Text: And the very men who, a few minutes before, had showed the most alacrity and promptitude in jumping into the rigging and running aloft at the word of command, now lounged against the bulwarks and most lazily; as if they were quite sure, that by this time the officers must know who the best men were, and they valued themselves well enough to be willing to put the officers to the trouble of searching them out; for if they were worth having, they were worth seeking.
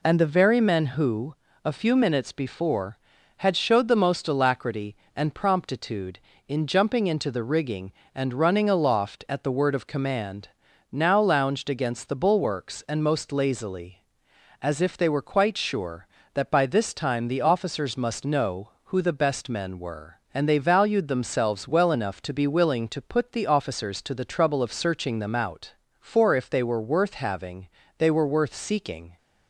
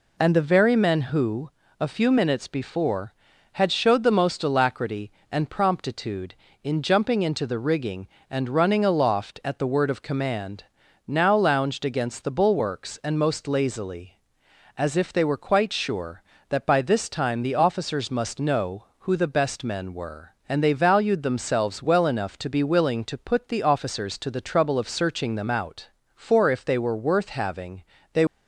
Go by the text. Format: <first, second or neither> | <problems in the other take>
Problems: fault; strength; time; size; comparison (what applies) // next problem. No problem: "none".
first | stops before "were worth seeking"; at 28.2 s